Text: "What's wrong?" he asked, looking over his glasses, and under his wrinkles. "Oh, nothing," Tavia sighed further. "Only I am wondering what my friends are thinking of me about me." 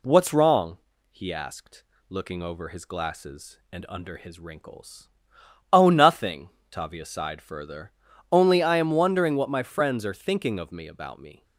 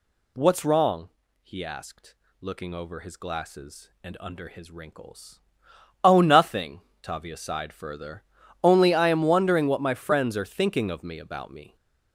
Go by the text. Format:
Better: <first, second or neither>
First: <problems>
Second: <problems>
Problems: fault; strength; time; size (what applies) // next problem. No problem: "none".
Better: first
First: none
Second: gets louder; strong; throughout; 7 dB